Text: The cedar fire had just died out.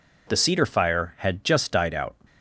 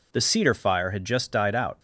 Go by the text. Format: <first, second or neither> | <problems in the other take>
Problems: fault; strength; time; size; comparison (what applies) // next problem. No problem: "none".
neither | none